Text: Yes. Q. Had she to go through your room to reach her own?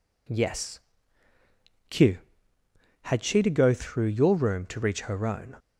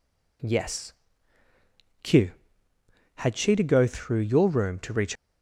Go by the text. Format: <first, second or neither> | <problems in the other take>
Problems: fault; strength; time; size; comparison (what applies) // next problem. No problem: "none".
first | stops before "her own"; at 5.1 s